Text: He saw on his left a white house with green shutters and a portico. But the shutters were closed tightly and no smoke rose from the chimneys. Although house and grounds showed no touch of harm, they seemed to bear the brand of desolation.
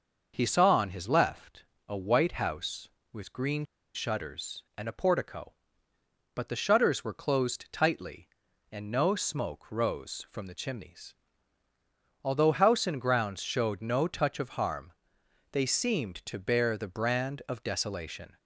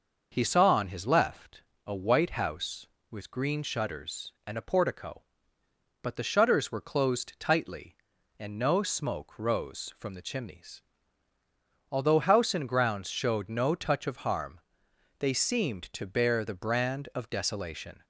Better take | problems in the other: second | starts louder than the rest; noticeable; until 1.3 s; 6 dB // pauses between "left" and "a"; slight; at 1.6 s; 0.24 s long; slight in the second // pauses between "green" and "shutters"; slight; at 3.6 s; 0.29 s long

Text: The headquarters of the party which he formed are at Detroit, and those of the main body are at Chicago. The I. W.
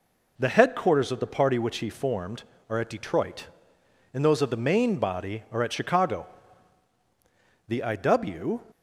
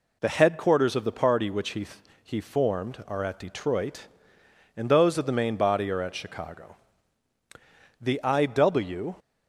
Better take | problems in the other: first | says "he" twice; at 2.2 s

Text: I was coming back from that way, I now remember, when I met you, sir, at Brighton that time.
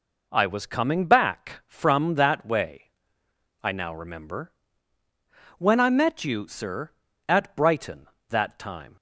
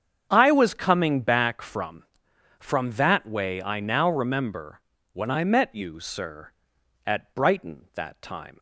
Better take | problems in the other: first | starts louder than the rest; strong; until 1.3 s; 7.5 dB // says "from" twice; at 2.5 s

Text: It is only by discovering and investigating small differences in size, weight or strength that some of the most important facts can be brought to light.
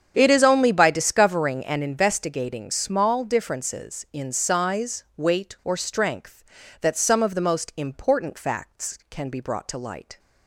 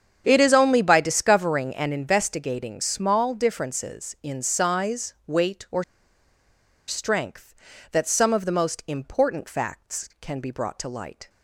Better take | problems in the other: first | starts louder than the rest; strong; until 1.2 s; 8 dB; strong in the first // pauses between "or" and "strength"; at 5.8 s; 1.0 s long

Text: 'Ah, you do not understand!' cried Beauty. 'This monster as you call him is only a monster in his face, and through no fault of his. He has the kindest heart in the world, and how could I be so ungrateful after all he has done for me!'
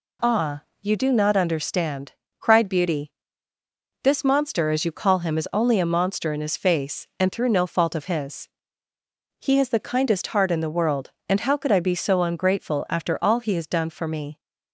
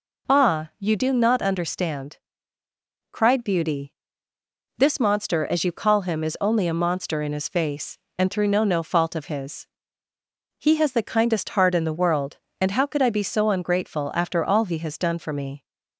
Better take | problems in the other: first | says "no" twice; at 8.6 s

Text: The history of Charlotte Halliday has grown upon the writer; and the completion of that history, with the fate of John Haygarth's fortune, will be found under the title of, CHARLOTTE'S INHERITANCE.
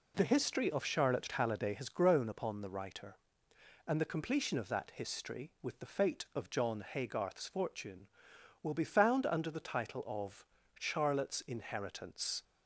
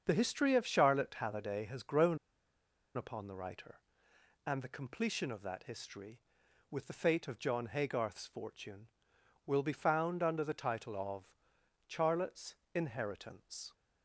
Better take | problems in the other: first | starts louder than the rest; until 1.0 s; 7 dB // pauses between "grown" and "upon"; noticeable; at 2.1 s; 0.77 s long // pauses between "CHARLOTTE'S" and "INHERITANCE"; slight; at 12.5 s; 0.18 s long

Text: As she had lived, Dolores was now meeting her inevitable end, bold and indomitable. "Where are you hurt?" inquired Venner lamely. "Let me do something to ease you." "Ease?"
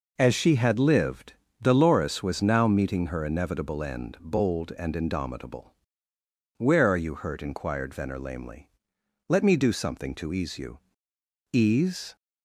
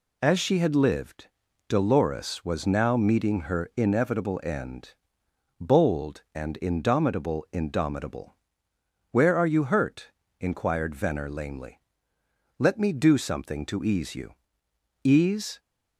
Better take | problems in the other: first | says "indomitable" twice; at 7.5 s

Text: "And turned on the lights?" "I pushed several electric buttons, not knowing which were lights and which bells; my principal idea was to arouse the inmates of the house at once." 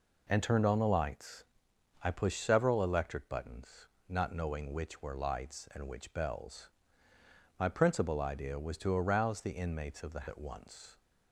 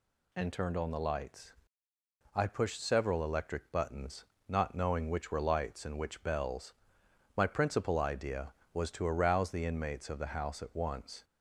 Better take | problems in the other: second | skips "house"; at 10.2 s

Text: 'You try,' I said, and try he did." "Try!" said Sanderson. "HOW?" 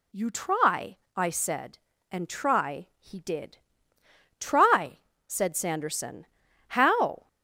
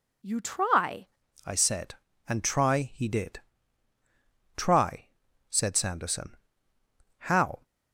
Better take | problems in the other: first | changes voice at "I"; from 1.4 s on; 6.2 s long

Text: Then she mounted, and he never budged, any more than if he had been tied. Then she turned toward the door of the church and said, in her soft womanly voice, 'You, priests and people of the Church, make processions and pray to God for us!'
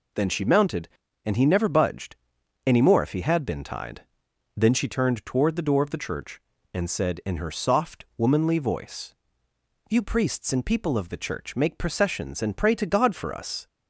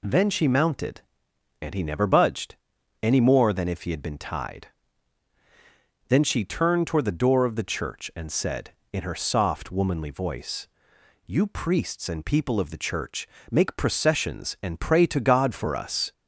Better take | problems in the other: second | skips "than"; at 3.0 s

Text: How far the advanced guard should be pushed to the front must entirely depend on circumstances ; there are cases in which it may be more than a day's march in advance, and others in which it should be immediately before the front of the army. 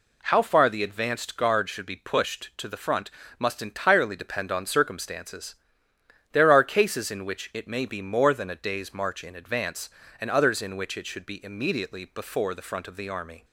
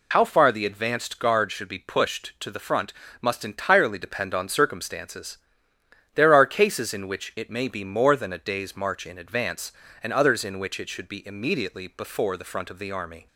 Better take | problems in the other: first | loses the start of "How"; at 0.1 s; 60 ms // pauses between "front" and "must"; slight; at 2.9 s; 0.28 s long; slight in the first

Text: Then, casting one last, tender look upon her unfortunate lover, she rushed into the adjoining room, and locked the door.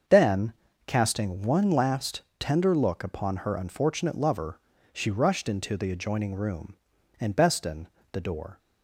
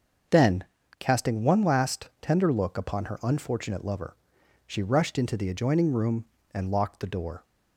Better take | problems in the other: second | starts louder than the rest; until 1.4 s; 6.5 dB; also in the second // says "beston" for "locked"; at 7.3 s

